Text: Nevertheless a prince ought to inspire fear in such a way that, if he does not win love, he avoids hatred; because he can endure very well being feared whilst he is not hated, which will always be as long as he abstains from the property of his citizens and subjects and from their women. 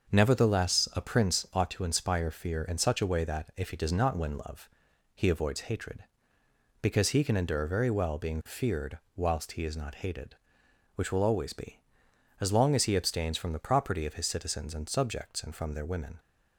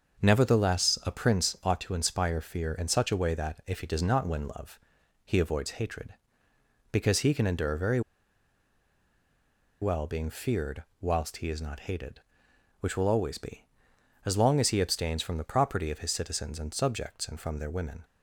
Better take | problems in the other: first | starts louder than the rest; until 1.2 s; 6.5 dB; also in the first // pauses between "very" and "well"; strong; at 8.0 s; 1.8 s long // pauses between "feared" and "whilst"; slight; at 10.8 s; 0.18 s long; slight in the first

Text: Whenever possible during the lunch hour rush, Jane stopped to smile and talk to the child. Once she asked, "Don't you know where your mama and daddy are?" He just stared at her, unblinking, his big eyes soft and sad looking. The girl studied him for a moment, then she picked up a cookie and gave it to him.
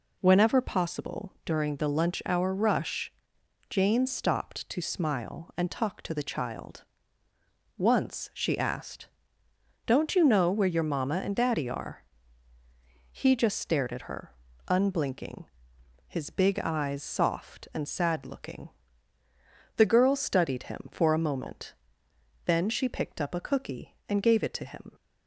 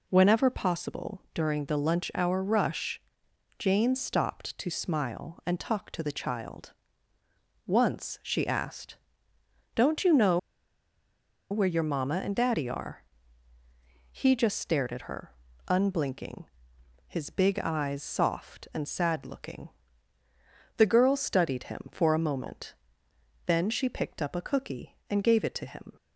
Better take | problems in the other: first | pauses between "know" and "where"; at 10.3 s; 1.1 s long

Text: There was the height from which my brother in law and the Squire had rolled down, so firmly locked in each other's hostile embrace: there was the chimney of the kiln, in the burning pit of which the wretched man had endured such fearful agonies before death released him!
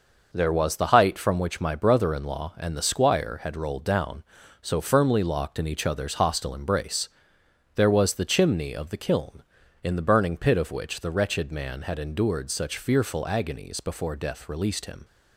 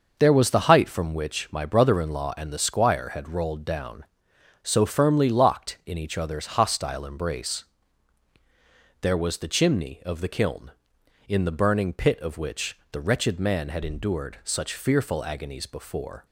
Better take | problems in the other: first | starts louder than the rest; until 1.2 s; 6 dB // stops before "death released him"; at 16.2 s

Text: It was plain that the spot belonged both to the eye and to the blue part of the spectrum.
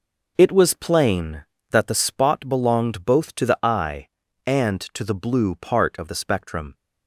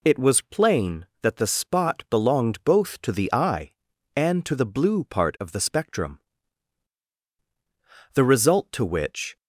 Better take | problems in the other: first | goes on to say "The result to which"; noticeable; from 8.1 s on; 1.2 s long

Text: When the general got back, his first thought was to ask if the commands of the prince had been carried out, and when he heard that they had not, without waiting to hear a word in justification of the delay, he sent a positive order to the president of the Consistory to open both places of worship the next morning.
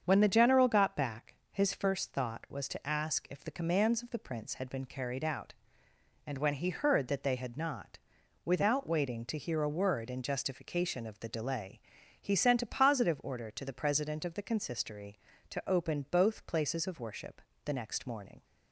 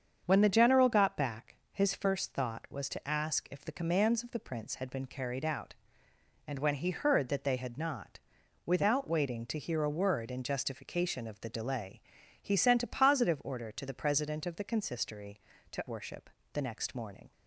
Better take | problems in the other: first | starts louder than the rest; strong; until 1.2 s; 7.5 dB; strong in the first // skips "open both places of"; at 15.8 s // pauses between "worship" and "the"; slight; at 16.2 s; 0.22 s long; slight in the first

